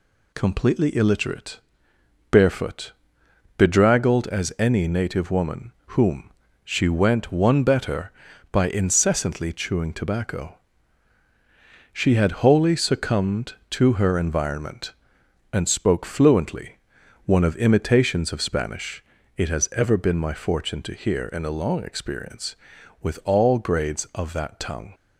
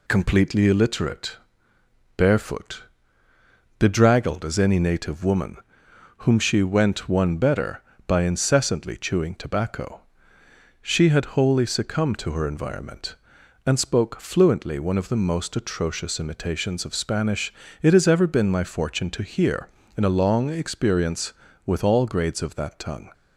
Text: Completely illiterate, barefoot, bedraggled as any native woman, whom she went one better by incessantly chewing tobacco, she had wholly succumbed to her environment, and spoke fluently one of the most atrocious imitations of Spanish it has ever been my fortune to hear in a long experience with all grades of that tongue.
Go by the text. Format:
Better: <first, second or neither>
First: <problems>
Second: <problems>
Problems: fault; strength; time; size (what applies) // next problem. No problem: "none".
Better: second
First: pauses between "whom" and "she"; slight; at 6.3 s; 0.34 s long // pauses between "fluently" and "one"; noticeable; at 16.7 s; 0.48 s long // skips "the most atrocious"; at 17.5 s // pauses between "Spanish" and "it"; slight; at 19.0 s; 0.34 s long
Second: pauses between "Spanish" and "it"; slight; at 17.5 s; 0.30 s long